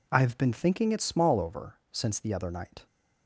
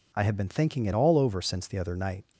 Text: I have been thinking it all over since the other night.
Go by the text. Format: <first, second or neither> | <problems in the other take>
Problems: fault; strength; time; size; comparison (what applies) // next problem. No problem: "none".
second | says "small" for "all"; at 1.0 s